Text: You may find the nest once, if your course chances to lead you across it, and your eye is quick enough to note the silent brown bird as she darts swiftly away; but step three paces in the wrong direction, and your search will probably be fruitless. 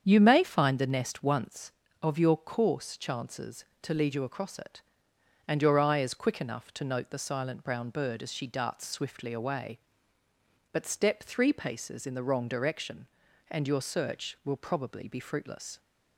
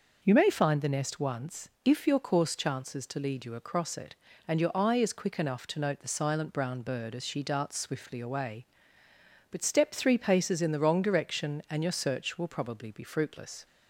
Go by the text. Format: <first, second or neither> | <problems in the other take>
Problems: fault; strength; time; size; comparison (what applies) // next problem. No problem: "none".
second | starts louder than the rest; strong; until 1.0 s; 7.5 dB // says "of" for "if"; at 2.0 s